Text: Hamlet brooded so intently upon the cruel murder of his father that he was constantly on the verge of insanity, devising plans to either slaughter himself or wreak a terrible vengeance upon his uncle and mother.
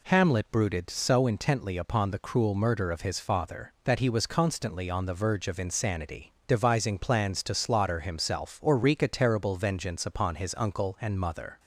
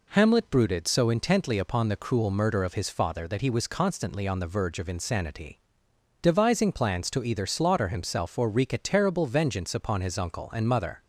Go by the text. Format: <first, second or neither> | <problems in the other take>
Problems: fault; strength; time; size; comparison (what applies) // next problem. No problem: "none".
second | skips "either"; at 7.5 s